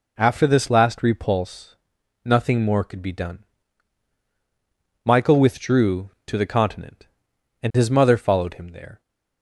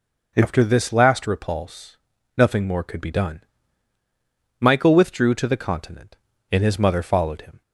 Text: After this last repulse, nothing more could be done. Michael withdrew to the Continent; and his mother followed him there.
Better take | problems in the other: first | stops before "there"; at 7.6 s

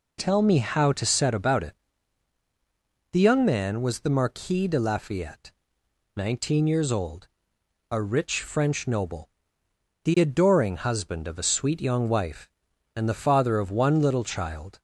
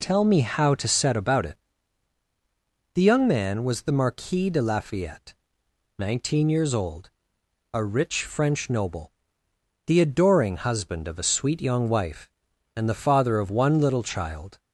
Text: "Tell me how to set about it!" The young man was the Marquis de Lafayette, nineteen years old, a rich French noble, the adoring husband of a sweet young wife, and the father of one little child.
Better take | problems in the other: neither | none

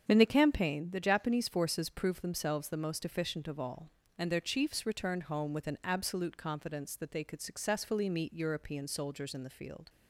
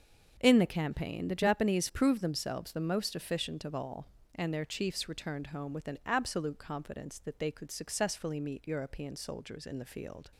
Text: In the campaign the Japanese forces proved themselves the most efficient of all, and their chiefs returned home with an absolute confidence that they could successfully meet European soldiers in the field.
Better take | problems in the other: first | starts louder than the rest; until 1.3 s; 6.5 dB; strong in the first // skips "forces"; at 1.8 s

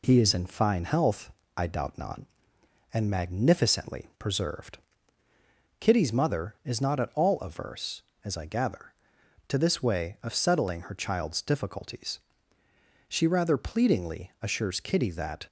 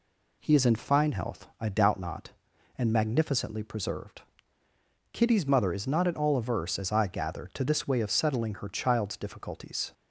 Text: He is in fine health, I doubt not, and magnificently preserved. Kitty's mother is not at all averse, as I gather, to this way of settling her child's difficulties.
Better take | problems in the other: second | goes on to say "She rather pleadingly assures Kitty that"; strong; from 13.0 s on; 2.3 s long

